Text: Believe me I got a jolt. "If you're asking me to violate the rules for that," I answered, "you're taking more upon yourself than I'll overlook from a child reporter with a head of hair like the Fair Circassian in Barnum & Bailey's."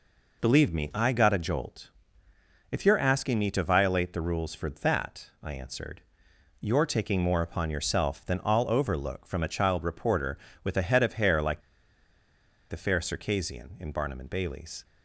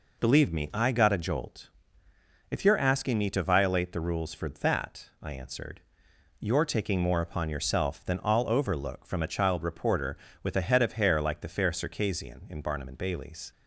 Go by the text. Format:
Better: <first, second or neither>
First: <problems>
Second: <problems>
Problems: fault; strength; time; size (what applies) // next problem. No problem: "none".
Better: second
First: pauses between "like" and "the"; at 11.5 s; 1.0 s long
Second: none